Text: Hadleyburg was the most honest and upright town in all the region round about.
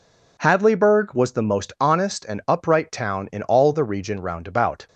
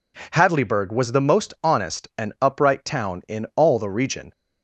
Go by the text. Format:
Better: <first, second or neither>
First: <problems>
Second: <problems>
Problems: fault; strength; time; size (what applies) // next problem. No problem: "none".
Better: first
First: none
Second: stops before "round about"; at 4.3 s